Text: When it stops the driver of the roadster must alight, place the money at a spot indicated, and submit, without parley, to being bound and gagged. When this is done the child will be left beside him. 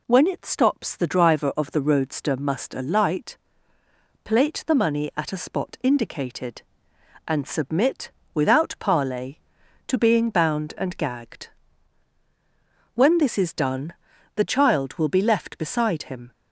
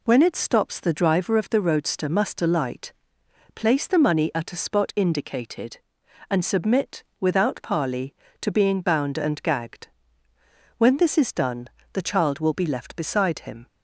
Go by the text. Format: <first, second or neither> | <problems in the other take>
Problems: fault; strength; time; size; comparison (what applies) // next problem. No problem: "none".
second | says "plate" for "place"; at 4.2 s // pauses between "done" and "the"; at 13.9 s; 0.42 s long; slight in the second